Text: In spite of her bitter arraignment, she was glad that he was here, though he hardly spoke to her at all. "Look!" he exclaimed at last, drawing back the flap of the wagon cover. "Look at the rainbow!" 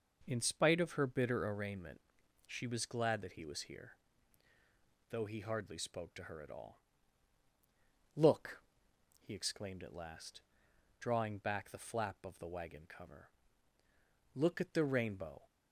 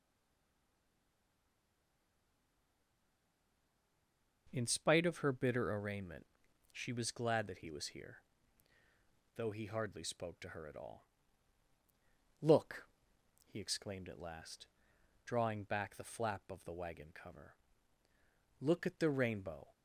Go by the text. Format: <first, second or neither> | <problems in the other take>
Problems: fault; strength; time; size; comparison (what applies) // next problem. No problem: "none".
first | stays silent before the first word; strong; until 4.4 s; 4.4 s long